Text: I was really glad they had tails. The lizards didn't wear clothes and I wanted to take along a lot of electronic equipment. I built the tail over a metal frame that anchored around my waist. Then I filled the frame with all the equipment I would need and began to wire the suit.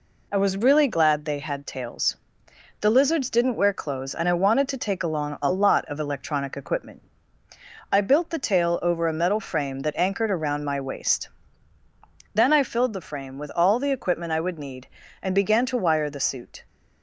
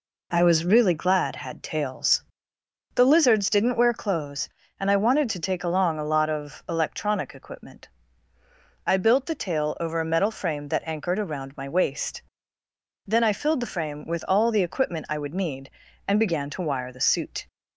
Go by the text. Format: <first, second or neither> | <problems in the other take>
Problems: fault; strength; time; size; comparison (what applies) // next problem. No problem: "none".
first | skips "they"; at 1.3 s